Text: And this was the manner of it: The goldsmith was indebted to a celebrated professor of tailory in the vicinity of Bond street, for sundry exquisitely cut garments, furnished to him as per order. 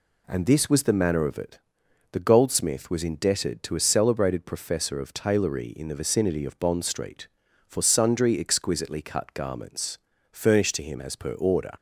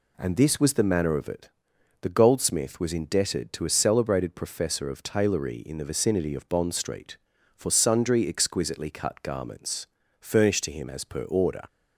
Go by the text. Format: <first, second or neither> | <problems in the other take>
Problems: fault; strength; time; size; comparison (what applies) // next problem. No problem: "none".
neither | none